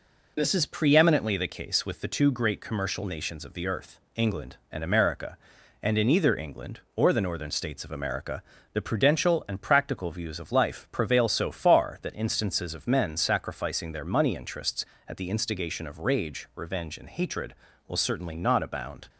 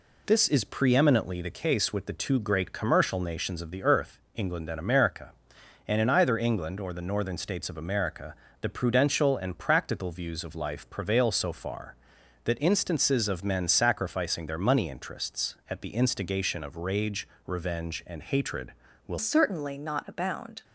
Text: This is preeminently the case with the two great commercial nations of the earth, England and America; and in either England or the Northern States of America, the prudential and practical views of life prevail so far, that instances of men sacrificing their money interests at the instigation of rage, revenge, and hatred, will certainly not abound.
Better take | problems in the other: first | changes voice at "certainly"; from 19.1 s on; 1.5 s long

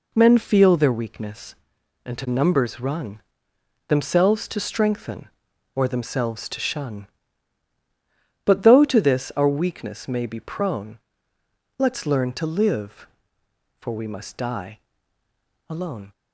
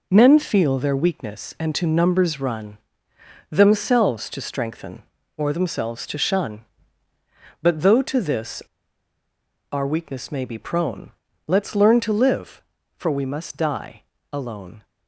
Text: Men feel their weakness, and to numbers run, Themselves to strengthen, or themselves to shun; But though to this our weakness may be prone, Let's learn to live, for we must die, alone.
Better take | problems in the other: first | pauses between "this" and "our"; at 8.6 s; 1.1 s long

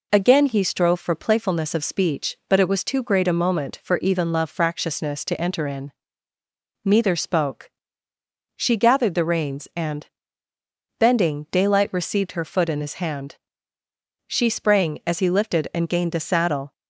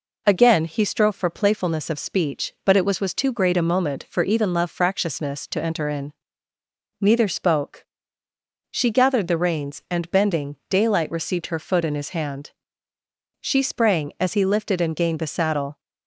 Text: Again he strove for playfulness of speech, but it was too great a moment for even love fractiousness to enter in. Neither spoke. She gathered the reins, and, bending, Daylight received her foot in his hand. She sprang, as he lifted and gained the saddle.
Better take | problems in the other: first | says "was" twice; at 2.9 s

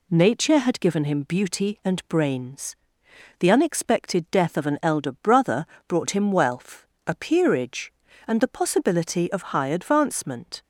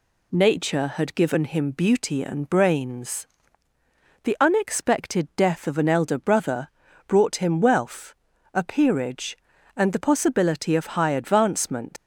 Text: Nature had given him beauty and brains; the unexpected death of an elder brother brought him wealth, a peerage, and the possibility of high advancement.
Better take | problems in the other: first | pauses between "brother" and "brought"; at 6.6 s; 0.40 s long; slight in the first // leaves "advancement" unfinished; at 11.9 s; 120 ms

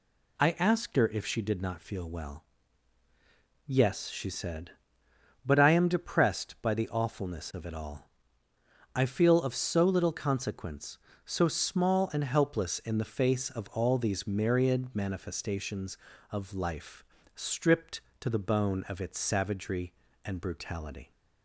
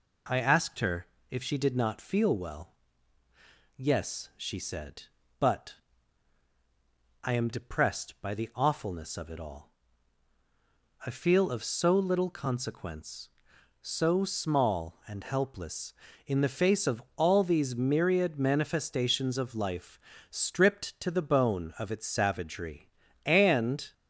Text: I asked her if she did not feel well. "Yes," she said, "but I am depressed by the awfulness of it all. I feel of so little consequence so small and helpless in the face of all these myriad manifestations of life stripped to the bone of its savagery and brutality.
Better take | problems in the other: first | pauses between "her" and "if"; slight; at 1.0 s; 0.26 s long // pauses between "but" and "I"; strong; at 5.7 s; 1.4 s long // pauses between "life" and "stripped"; slight; at 19.9 s; 0.32 s long; slight in the first // stops before "brutality"; at 23.9 s

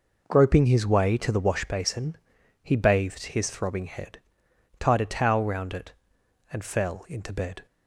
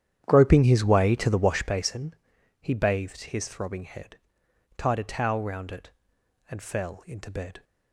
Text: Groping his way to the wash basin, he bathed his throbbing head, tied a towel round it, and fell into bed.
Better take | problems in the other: first | starts louder than the rest; strong; until 2.0 s; 10 dB

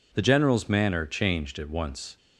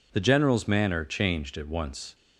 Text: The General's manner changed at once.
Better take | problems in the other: neither | none

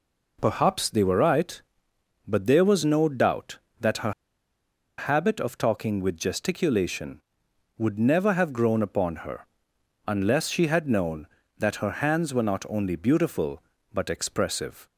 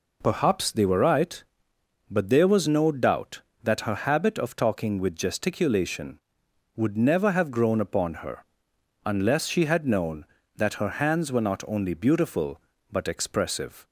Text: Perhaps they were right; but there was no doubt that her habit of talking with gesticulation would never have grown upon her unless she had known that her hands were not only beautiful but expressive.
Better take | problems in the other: second | pauses between "her" and "habit"; noticeable; at 4.1 s; 0.86 s long // pauses between "her" and "unless"; noticeable; at 9.4 s; 0.60 s long; noticeable in the second

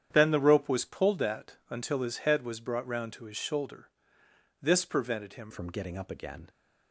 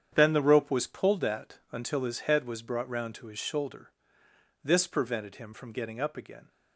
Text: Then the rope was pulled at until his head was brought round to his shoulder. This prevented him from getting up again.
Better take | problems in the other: second | starts louder than the rest; strong; until 1.1 s; 9 dB; strong in the second // changes voice at "from"; from 5.5 s on; 0.9 s long

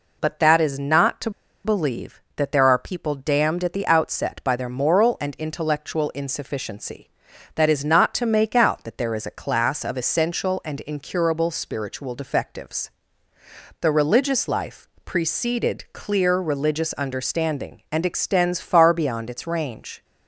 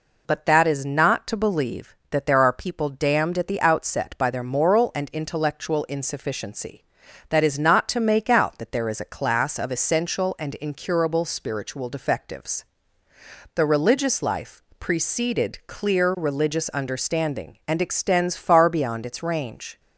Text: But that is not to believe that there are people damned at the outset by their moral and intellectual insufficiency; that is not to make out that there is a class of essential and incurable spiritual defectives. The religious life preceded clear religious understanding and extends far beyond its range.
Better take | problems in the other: second | pauses between "to" and "believe"; slight; at 1.2 s; 0.34 s long // pauses between "life" and "preceded"; slight; at 14.8 s; 0.18 s long; slight in the second

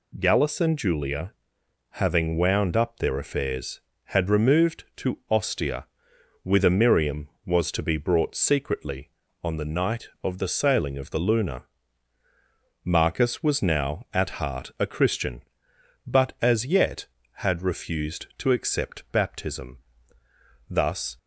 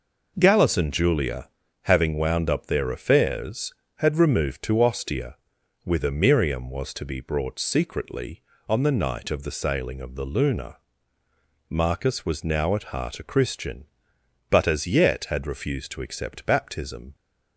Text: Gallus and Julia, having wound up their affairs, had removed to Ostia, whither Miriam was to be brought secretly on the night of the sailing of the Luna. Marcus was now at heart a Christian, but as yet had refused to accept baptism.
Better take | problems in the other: second | goes on to say "Thus"; slight; from 20.6 s on; 0.48 s long

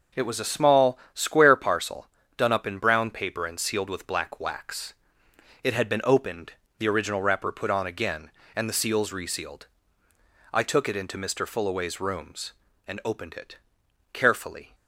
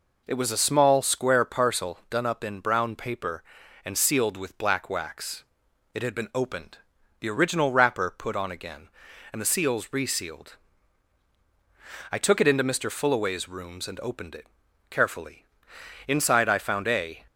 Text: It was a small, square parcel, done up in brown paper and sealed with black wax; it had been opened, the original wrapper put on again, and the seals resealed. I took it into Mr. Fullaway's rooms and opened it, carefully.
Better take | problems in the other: first | goes on to say "Inside I found a"; noticeable; from 16.1 s on; 1.0 s long

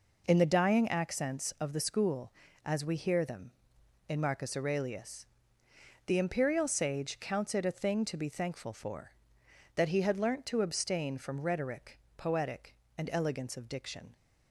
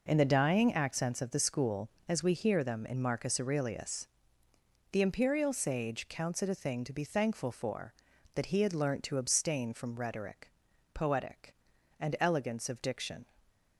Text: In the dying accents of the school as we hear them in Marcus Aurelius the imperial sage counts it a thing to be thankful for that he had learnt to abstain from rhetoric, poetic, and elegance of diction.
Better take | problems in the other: neither | pauses between "Aurelius" and "the"; noticeable; the same in both

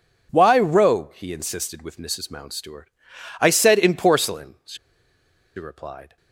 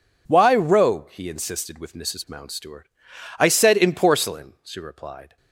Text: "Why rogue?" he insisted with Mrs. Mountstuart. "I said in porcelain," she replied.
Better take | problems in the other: second | pauses between "she" and "replied"; noticeable; at 4.7 s; 0.80 s long

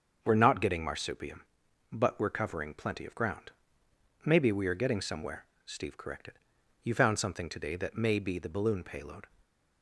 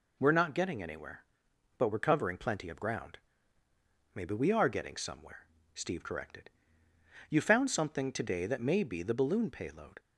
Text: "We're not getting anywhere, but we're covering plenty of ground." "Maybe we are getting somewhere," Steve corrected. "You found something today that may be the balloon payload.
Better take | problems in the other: second | starts louder than the rest; until 1.2 s; 6.5 dB // says "marsupium" for "anywhere"; at 0.8 s // stays silent after the last word; slight; from 9.2 s on; 0.6 s long

